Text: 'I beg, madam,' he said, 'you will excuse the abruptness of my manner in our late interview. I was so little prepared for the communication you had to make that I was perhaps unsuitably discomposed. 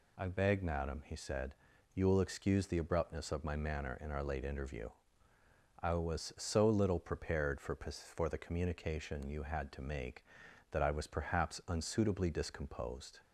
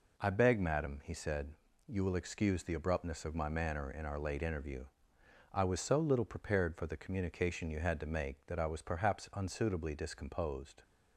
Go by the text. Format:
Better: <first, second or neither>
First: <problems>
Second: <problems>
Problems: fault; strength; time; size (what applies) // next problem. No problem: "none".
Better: second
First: says "for" twice; at 7.7 s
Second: none